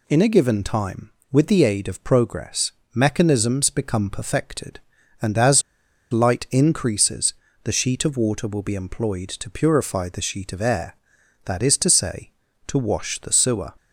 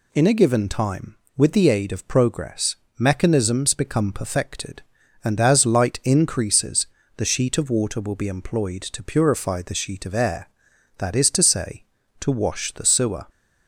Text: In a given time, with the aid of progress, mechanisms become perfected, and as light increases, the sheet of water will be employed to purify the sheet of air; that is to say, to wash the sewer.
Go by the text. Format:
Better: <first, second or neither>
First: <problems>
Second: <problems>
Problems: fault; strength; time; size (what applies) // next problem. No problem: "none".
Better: second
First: pauses between "as" and "light"; noticeable; at 5.6 s; 0.50 s long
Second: none